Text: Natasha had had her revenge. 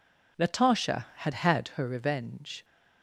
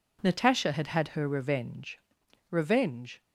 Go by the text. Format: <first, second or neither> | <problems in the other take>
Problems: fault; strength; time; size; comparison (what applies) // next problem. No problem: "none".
first | says "revenge" twice; at 2.5 s